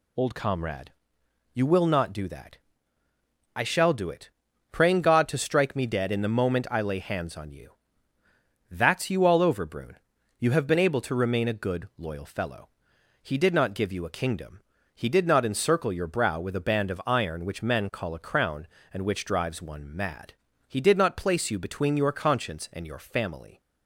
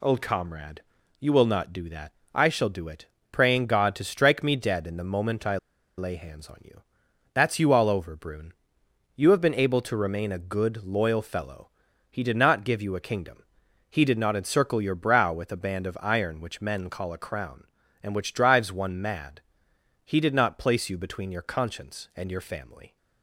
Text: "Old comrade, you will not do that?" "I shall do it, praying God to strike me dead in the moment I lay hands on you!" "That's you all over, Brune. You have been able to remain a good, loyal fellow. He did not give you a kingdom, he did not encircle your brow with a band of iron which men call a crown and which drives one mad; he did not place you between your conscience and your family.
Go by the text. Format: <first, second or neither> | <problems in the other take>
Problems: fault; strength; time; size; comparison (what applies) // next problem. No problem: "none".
first | pauses between "I" and "lay"; at 5.5 s; 0.41 s long